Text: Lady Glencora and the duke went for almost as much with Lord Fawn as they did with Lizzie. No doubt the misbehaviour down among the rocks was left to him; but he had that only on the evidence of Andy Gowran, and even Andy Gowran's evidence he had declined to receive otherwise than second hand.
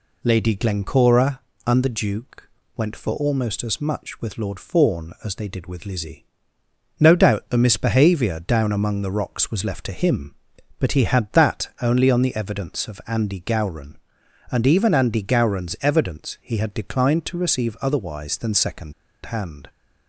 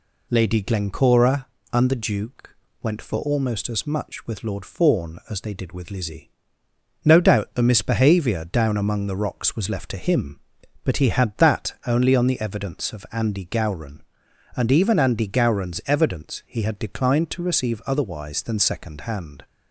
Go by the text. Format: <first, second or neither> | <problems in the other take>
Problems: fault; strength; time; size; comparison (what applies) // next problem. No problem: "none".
second | pauses between "duke" and "went"; slight; at 2.4 s; 0.26 s long; slight in the second // pauses between "second" and "hand"; slight; at 18.9 s; 0.32 s long